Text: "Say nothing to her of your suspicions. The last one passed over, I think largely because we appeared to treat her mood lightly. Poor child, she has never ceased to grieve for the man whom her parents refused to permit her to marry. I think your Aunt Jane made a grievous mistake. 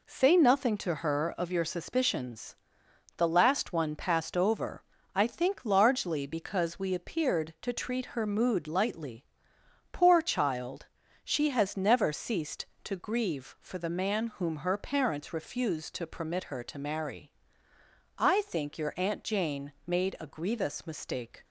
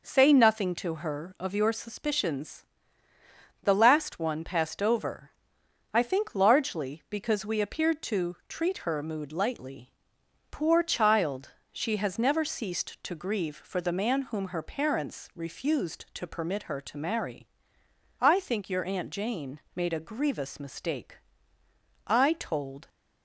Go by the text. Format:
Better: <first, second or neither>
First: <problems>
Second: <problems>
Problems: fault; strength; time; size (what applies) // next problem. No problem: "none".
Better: first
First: none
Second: pauses between "Jane" and "made"; slight; at 19.5 s; 0.16 s long // goes on to say "I told"; noticeable; from 22.0 s on; 0.82 s long